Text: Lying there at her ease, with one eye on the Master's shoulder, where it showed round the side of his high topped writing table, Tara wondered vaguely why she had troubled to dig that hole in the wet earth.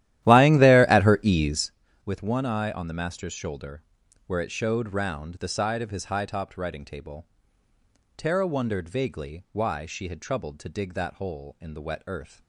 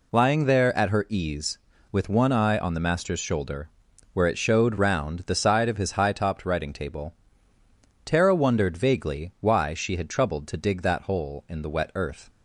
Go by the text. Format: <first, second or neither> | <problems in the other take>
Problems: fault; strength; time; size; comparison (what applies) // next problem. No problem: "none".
second | starts louder than the rest; strong; until 1.8 s; 13.5 dB